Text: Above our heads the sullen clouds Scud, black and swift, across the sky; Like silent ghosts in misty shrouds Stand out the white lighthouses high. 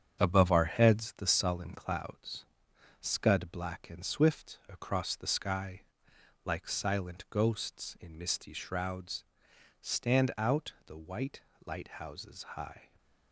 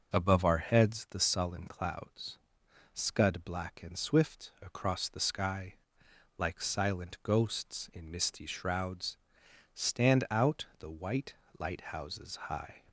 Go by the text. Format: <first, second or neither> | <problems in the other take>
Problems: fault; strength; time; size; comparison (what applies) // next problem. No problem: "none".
second | gets quieter; noticeable; throughout; 5.5 dB // pauses between "clouds" and "Scud"; noticeable; at 2.4 s; 0.56 s long; noticeable in the second // pauses between "shrouds" and "Stand"; noticeable; at 9.2 s; 0.56 s long; noticeable in the second // pauses between "white" and "lighthouses"; slight; at 11.3 s; 0.26 s long; slight in the second